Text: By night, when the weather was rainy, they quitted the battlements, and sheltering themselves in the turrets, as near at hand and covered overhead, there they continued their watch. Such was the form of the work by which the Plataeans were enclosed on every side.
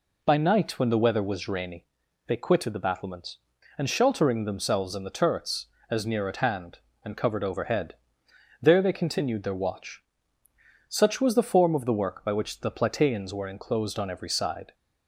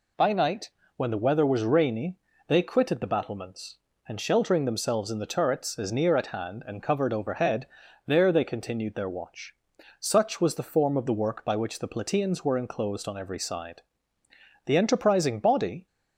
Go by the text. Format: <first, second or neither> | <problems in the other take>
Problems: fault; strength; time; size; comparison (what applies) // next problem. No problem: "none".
first | goes on to say "The enterprising body"; noticeable; from 14.6 s on; 1.2 s long